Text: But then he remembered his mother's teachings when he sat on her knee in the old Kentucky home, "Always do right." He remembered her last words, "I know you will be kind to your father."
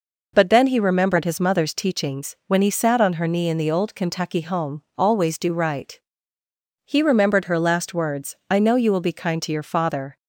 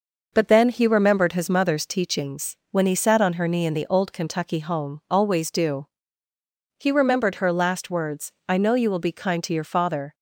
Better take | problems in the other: first | skips "right"; at 6.3 s

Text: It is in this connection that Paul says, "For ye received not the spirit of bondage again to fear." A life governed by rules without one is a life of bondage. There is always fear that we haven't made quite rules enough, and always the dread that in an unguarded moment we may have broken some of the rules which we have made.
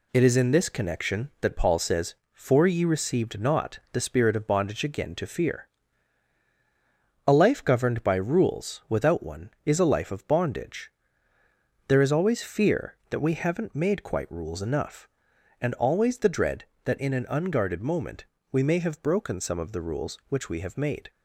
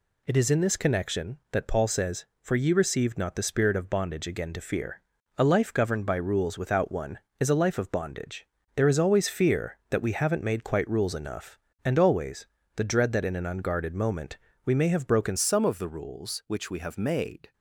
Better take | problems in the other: first | pauses between "always" and "the"; slight; at 12.4 s; 0.30 s long // pauses between "moment" and "we"; slight; at 14.3 s; 0.26 s long; slight in the first // changes voice at "some"; from 15.3 s on; 2.2 s long

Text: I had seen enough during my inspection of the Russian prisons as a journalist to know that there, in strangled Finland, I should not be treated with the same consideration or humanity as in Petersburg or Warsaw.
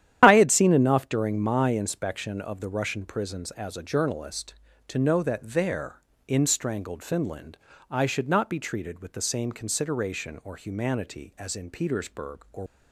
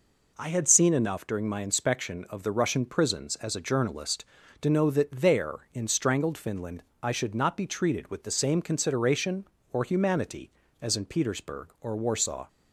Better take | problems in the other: second | starts louder than the rest; strong; until 1.2 s; 10.5 dB // stops before "Warsaw"; at 12.6 s

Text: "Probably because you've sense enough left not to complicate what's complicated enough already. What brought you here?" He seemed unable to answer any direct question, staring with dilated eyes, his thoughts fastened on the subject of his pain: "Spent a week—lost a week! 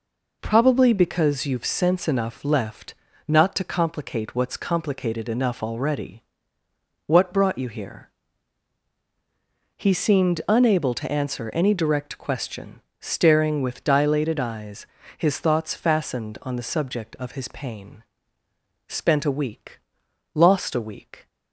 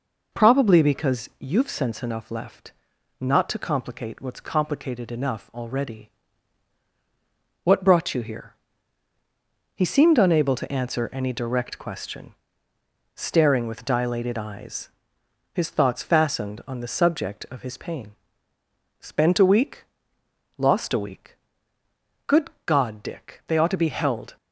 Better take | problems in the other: first | pauses between "left" and "not"; noticeable; at 2.7 s; 0.46 s long; slight in the first // goes on to say "Good God Dick they ought to be held"; strong; from 22.2 s on; 2.0 s long

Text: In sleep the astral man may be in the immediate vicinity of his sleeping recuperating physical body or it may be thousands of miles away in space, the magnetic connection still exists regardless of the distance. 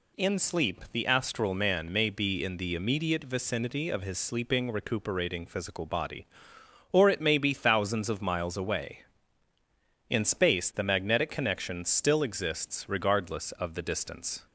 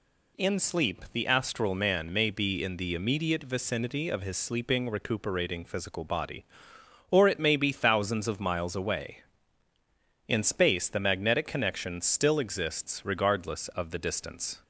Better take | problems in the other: neither | none

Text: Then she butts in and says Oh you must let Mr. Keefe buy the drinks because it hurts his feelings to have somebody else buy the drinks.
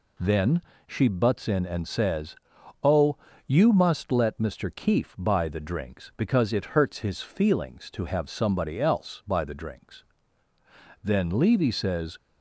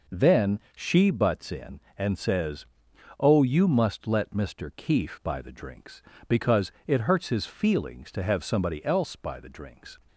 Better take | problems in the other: second | pauses between "Then" and "she"; slight; at 0.6 s; 0.26 s long; slight in the second // pauses between "says" and "Oh"; noticeable; at 2.3 s; 0.48 s long; noticeable in the second // pauses between "Oh" and "you"; slight; at 3.1 s; 0.30 s long // goes on to say "Then Levy says"; noticeable; from 11.0 s on; 1.1 s long

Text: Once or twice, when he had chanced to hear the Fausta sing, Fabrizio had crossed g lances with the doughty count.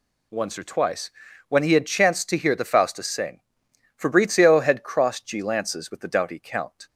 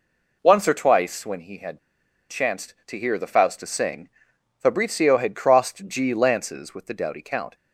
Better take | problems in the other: first | pauses between "had" and "chanced"; noticeable; at 1.7 s; 0.51 s long

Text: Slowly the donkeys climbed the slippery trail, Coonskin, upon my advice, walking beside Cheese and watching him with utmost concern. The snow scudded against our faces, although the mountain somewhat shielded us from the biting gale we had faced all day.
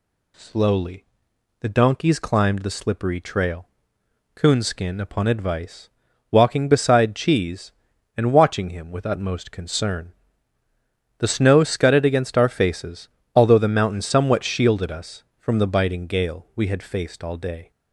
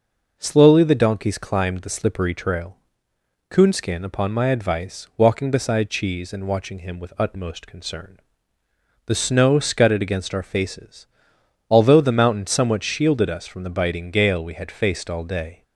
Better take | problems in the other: second | pauses between "Slowly" and "the"; noticeable; at 1.0 s; 0.56 s long // skips "my"; at 5.2 s

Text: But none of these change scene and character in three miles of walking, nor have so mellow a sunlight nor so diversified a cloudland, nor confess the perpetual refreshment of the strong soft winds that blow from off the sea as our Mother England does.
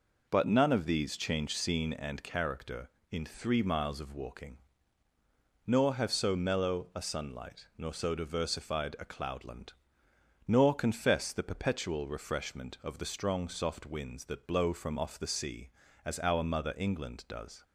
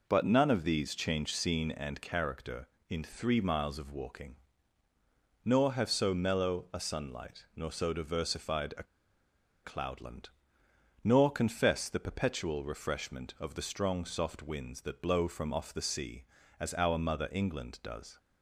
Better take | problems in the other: first | pauses between "a" and "cloudland"; noticeable; at 8.8 s; 0.80 s long

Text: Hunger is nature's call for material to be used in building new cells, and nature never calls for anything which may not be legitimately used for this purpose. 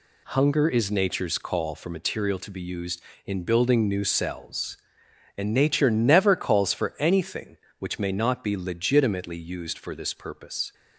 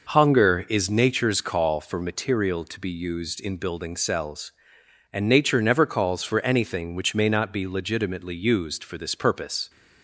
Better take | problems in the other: first | skips "new"; at 3.9 s

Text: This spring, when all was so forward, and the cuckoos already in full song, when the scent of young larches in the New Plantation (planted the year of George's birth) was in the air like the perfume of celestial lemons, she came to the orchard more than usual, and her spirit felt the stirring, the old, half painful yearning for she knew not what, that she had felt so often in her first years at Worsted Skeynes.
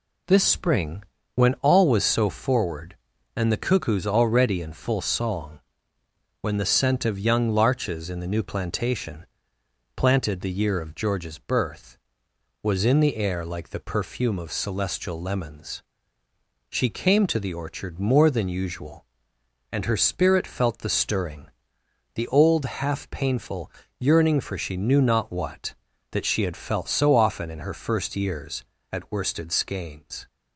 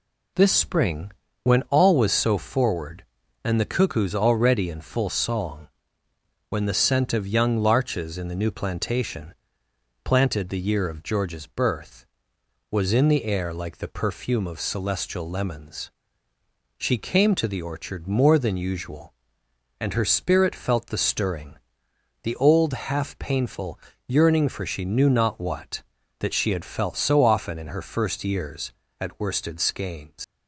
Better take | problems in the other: first | pauses between "painful" and "yearning"; slight; at 23.7 s; 0.30 s long; slight in the first // leaves "Skeynes" unfinished; at 30.2 s; 105 ms

